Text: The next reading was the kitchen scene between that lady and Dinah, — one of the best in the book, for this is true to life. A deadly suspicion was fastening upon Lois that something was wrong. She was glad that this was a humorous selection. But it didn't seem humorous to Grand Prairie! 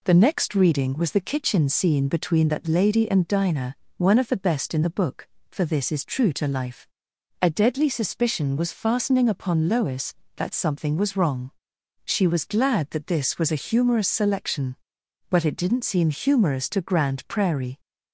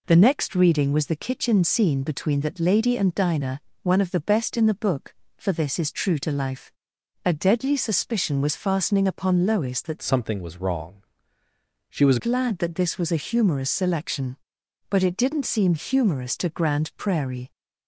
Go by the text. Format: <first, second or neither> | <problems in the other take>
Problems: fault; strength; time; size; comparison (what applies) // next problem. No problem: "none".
first | changes voice from "something" to "was"; from 10.0 to 12.1 s; 2.1 s long